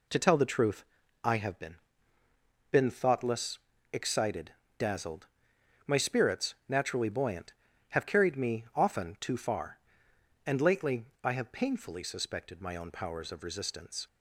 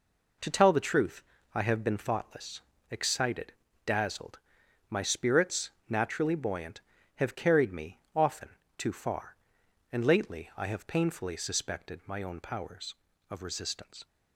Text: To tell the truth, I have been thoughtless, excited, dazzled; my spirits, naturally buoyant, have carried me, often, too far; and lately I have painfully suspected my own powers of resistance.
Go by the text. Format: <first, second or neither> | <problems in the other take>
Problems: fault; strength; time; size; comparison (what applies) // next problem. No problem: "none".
second | says "been" twice; at 2.6 s // pauses between "lately" and "I"; slight; at 11.0 s; 0.18 s long